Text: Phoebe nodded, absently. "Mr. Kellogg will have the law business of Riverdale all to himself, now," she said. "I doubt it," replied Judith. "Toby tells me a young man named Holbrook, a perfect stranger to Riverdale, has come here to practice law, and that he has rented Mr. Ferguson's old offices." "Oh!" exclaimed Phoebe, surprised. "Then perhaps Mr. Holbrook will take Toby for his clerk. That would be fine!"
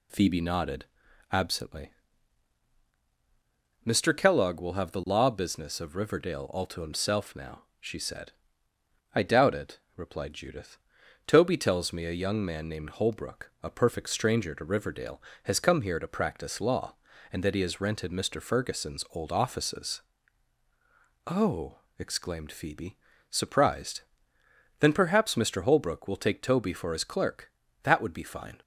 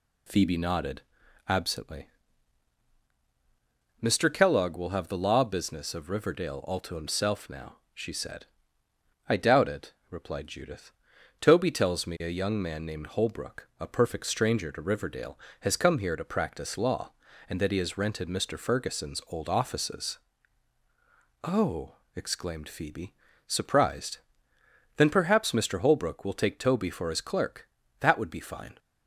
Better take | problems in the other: neither | none

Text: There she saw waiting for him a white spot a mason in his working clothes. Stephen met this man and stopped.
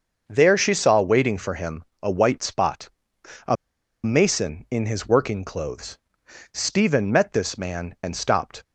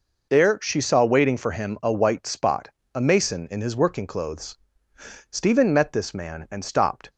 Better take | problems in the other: second | starts louder than the rest; until 1.2 s; 6.5 dB // pauses between "him" and "a"; slight; at 1.8 s; 0.18 s long // pauses between "spot" and "a"; noticeable; at 2.8 s; 0.56 s long; slight in the second // pauses between "a" and "mason"; noticeable; at 3.5 s; 0.48 s long

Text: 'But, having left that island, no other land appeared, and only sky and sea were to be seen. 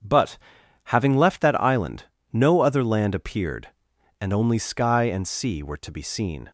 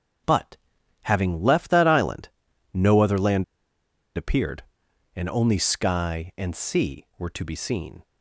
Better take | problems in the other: first | starts louder than the rest; strong; until 1.7 s; 7 dB; strong in the first // pauses between "land" and "appeared"; noticeable; at 3.4 s; 0.72 s long

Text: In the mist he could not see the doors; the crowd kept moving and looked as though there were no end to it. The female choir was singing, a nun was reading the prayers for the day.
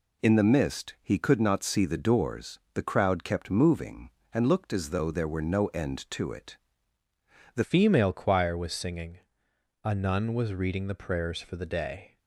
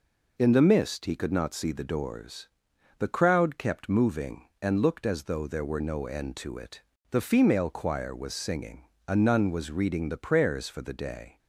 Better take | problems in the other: second | changes voice at "female"; from 7.6 s on; 4.5 s long

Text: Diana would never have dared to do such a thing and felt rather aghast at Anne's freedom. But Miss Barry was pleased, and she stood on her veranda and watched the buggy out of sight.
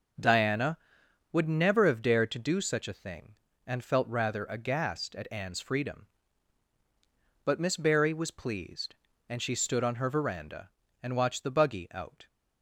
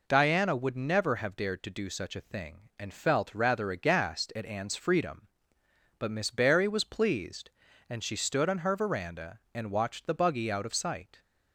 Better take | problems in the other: second | starts louder than the rest; noticeable; until 1.7 s; 6 dB // stops before "of sight"; at 12.2 s

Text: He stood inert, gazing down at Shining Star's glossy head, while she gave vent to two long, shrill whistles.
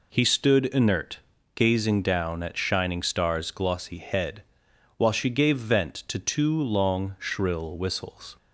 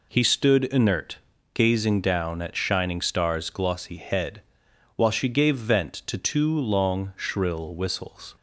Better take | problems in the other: neither | none

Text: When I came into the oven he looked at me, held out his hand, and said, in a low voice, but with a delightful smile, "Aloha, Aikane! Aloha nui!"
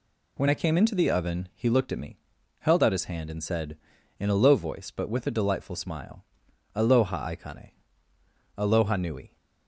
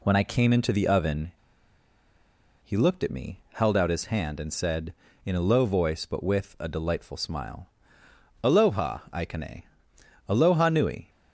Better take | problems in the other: first | pauses between "oven" and "he"; strong; at 1.3 s; 1.3 s long

